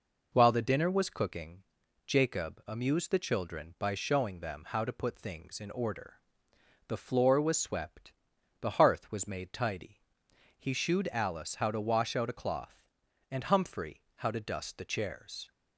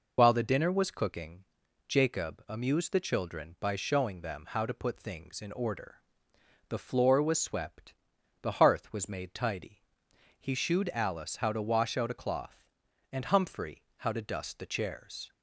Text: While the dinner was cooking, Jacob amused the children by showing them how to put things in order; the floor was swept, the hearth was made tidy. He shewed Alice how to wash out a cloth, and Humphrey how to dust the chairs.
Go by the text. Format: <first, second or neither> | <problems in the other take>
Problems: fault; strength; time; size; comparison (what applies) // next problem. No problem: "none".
first | loses the start of "While"; at 0.1 s; 40 ms